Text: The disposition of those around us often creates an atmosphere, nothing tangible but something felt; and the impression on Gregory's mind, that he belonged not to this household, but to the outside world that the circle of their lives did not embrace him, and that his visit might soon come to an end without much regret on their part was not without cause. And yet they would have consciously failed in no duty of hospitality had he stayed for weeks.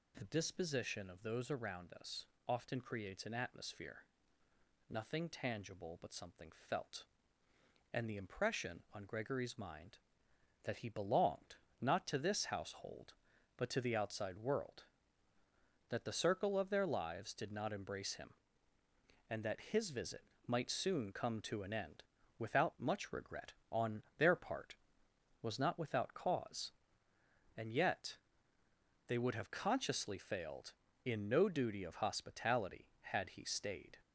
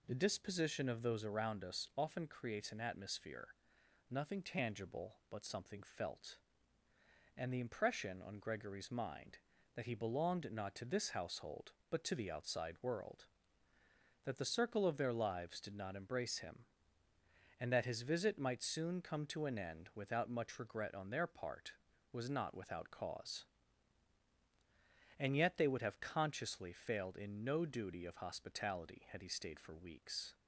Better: second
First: pauses between "us" and "often"; slight; at 2.2 s; 0.24 s long // pauses between "something" and "felt"; slight; at 6.4 s; 0.22 s long // pauses between "belonged" and "not"; slight; at 11.5 s; 0.26 s long // pauses between "visit" and "might"; slight; at 20.2 s; 0.26 s long // pauses between "end" and "without"; at 22.0 s; 0.38 s long // pauses between "on" and "their"; slight; at 24.0 s; 0.16 s long // pauses between "yet" and "they"; noticeable; at 28.1 s; 0.92 s long // stops before "for weeks"; at 34.0 s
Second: none

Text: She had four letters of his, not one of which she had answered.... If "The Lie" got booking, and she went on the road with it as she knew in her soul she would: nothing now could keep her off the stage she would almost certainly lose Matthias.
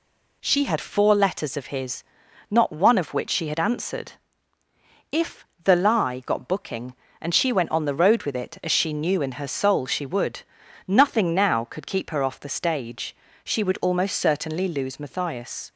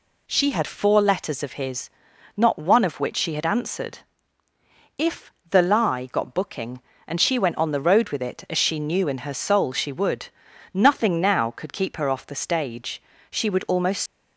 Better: first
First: pauses between "If" and "The"; slight; at 5.4 s; 0.20 s long // pauses between "stage" and "she"; slight; at 13.1 s; 0.28 s long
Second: pauses between "If" and "The"; slight; at 5.3 s; 0.20 s long // pauses between "stage" and "she"; slight; at 13.0 s; 0.28 s long // stops before "certainly lose Matthias"; at 14.0 s

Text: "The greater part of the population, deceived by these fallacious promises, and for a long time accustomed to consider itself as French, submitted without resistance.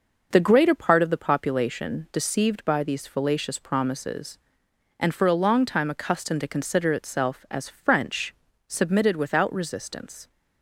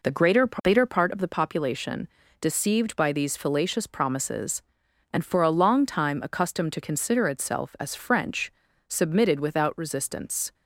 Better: first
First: none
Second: says "greater" twice; at 0.4 s

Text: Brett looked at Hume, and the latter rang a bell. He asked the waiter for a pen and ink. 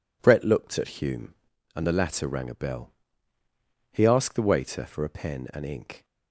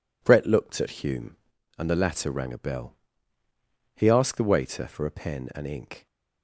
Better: neither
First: none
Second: none

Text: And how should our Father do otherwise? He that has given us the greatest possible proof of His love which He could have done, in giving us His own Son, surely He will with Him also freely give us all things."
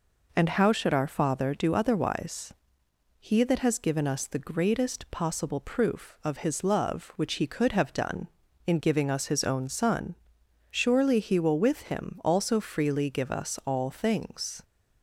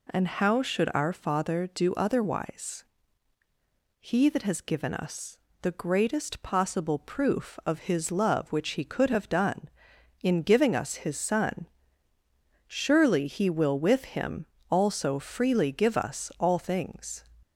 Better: first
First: none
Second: pauses between "us" and "the"; slight; at 5.3 s; 0.24 s long // skips "own"; at 11.1 s // pauses between "Him" and "also"; slight; at 14.4 s; 0.23 s long

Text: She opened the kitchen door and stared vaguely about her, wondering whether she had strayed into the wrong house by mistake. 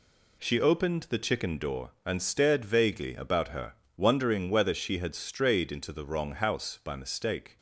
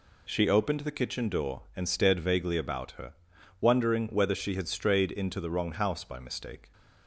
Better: second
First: says "chicken" for "kitchen"; at 1.1 s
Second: none

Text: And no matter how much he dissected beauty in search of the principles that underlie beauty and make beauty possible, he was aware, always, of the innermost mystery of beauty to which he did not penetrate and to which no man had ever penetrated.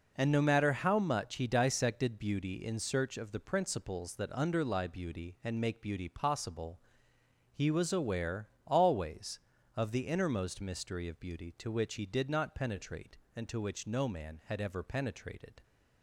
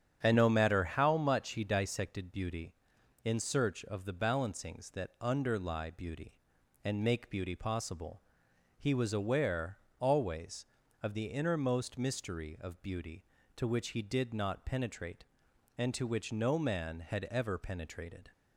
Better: first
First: none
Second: starts louder than the rest; strong; until 1.2 s; 8.5 dB // says "balancings" for "principles"; at 4.1 s

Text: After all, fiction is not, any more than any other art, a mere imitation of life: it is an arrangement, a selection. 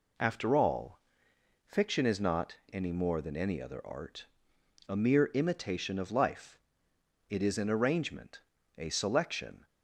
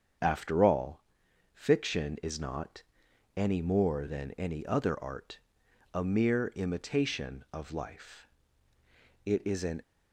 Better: first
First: none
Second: starts louder than the rest; until 1.7 s; 7 dB // stops before "arrangement a selection"; at 9.8 s

